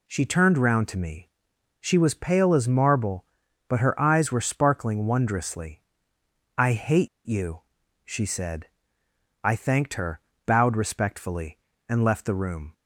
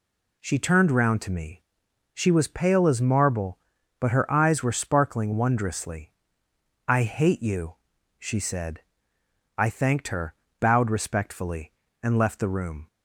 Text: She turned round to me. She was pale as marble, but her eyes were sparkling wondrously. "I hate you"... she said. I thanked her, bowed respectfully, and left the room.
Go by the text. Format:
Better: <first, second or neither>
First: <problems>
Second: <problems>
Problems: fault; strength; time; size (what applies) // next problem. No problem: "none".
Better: second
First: pauses between "hate" and "you"; slight; at 7.0 s; 0.18 s long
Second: none